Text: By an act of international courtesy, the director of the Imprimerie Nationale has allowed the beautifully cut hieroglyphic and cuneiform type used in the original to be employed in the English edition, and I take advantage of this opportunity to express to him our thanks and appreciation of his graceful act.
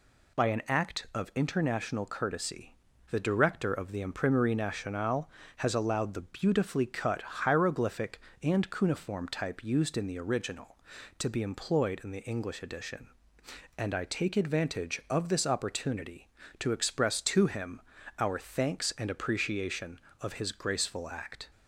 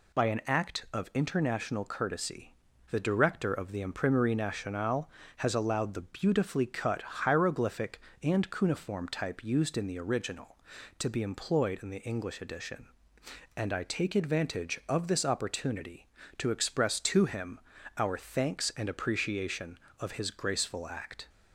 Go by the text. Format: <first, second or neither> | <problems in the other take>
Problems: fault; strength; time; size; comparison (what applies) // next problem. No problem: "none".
neither | pauses between "him" and "our"; slight; the same in both